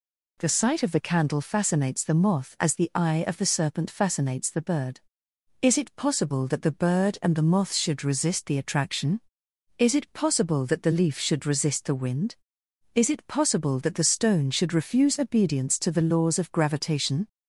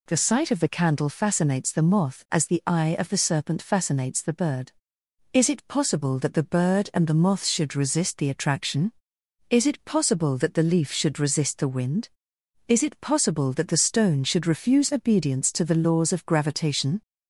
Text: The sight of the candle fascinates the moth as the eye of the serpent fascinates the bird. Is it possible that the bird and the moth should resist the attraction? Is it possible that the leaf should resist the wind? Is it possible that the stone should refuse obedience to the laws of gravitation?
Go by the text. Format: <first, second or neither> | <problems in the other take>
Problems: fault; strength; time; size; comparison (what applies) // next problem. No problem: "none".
neither | none